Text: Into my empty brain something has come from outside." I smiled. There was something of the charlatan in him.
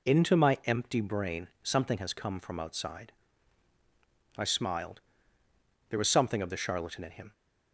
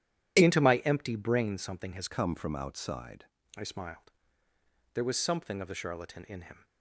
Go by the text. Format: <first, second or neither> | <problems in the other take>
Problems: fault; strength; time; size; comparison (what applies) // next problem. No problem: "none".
first | changes voice from "come" to "outside"; from 2.0 to 3.2 s; 1.2 s long